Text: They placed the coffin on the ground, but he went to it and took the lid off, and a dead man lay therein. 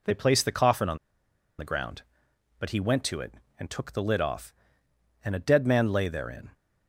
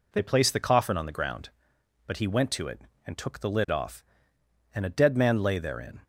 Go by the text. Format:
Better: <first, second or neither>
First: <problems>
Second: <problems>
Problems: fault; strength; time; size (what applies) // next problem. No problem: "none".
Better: second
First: pauses between "on" and "the"; noticeable; at 0.9 s; 0.61 s long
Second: none